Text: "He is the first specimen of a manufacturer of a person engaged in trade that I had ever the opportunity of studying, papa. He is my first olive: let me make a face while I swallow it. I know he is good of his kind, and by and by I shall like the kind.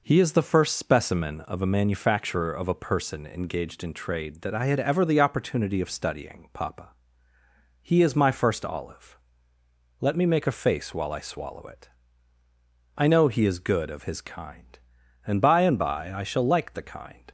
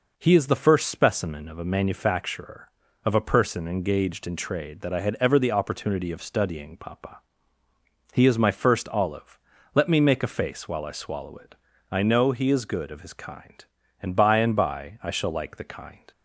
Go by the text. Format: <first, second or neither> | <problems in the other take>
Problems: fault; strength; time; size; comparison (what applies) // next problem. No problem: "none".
neither | none